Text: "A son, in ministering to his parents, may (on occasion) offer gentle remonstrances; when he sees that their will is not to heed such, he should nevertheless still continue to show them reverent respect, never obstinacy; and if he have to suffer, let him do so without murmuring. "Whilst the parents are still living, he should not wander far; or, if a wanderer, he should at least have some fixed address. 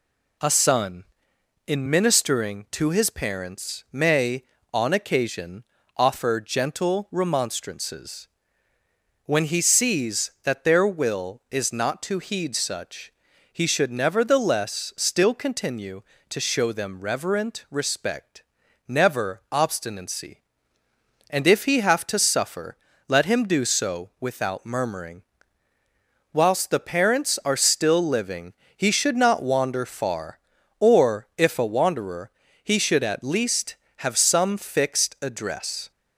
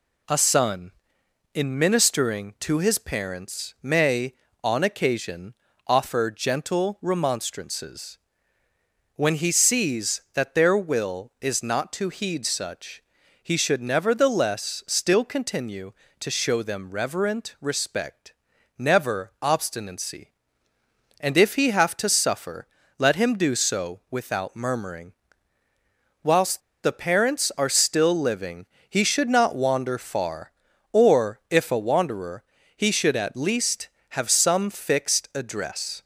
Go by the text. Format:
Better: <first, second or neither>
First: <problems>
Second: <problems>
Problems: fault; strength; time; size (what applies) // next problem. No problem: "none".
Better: first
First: none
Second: pauses between "Whilst" and "the"; slight; at 26.6 s; 0.22 s long